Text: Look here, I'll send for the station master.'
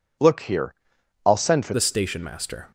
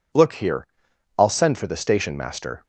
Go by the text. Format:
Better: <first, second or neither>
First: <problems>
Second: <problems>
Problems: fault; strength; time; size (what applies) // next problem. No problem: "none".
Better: second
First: changes voice at "the"; from 1.7 s on; 0.9 s long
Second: none